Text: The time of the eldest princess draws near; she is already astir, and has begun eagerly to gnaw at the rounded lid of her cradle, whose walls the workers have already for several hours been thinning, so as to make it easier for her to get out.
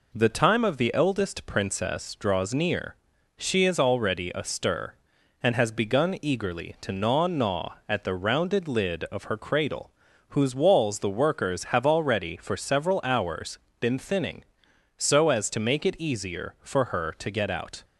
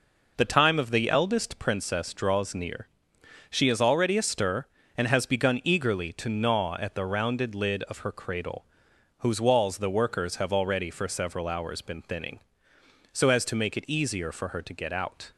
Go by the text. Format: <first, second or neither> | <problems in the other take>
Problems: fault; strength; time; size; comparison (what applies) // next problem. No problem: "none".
second | says "gnaw" twice; at 7.2 s // pauses between "hours" and "been"; slight; at 13.5 s; 0.22 s long